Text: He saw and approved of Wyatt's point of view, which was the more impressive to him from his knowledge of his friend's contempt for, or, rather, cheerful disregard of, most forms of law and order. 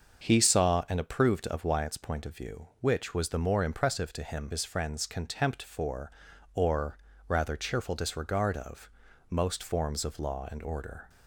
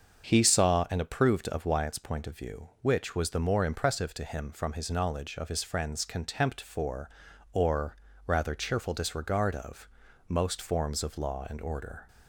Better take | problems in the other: second | starts louder than the rest; until 1.2 s; 6.5 dB; also in the second // skips "from his knowledge of"; at 4.5 s

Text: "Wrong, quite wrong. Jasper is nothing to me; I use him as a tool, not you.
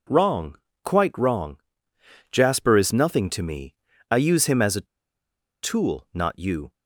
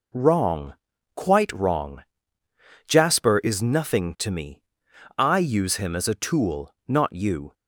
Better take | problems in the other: second | pauses between "a" and "tool"; noticeable; at 4.8 s; 0.76 s long

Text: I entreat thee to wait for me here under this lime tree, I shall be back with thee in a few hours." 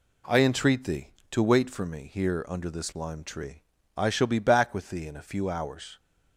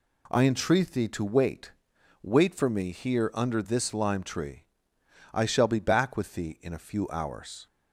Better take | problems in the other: first | says "wait" twice; at 2.2 s

